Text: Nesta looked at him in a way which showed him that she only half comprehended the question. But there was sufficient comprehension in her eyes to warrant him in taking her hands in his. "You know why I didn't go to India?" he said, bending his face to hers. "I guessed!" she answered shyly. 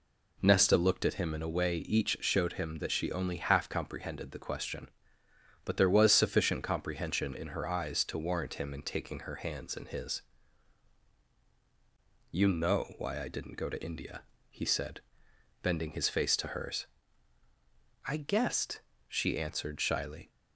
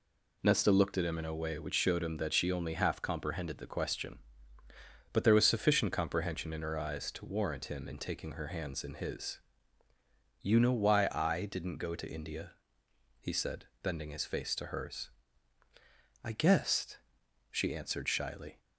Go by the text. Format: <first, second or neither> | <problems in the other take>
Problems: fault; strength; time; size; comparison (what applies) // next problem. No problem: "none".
second | says "each" for "which"; at 1.7 s